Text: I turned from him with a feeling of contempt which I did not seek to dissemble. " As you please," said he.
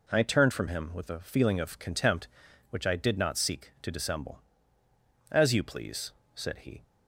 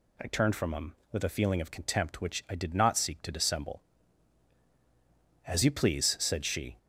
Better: first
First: none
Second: says "she" for "he"; at 6.4 s

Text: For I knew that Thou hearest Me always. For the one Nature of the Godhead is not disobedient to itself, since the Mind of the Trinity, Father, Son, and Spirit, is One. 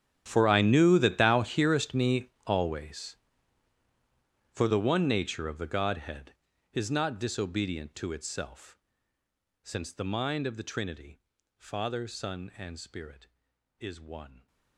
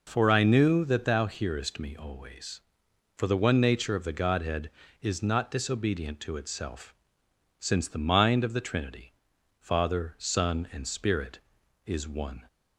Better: second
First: gets quieter; strong; throughout; 20.5 dB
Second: none

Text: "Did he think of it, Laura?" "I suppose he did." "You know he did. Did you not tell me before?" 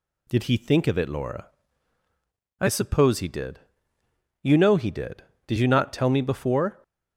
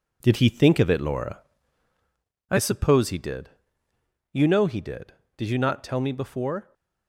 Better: first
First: none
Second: gets quieter; strong; throughout; 7.5 dB

